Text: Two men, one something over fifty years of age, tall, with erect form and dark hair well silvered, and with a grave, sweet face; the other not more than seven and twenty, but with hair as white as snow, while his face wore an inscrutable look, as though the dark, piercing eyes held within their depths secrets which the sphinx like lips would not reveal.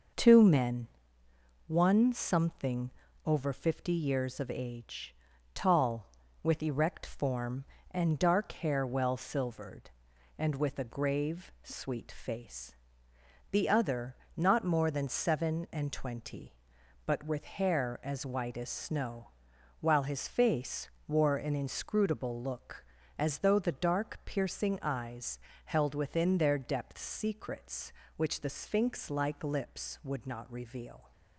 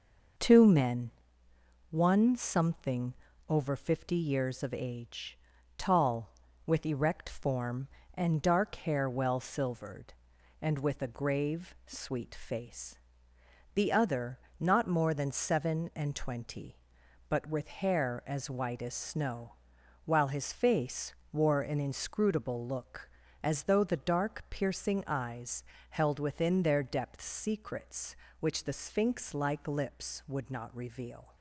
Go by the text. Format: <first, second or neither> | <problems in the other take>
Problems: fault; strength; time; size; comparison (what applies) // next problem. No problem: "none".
neither | starts louder than the rest; noticeable; the same in both // pauses between "something" and "over"; slight; the same in both // pauses between "other" and "not"; slight; the same in both // pauses between "face" and "wore"; slight; the same in both // pauses between "eyes" and "held"; slight; the same in both